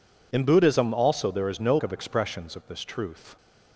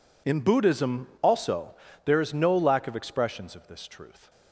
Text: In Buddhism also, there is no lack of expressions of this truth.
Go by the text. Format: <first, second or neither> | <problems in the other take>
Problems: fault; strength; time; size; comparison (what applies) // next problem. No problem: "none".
second | skips "lack"; at 1.7 s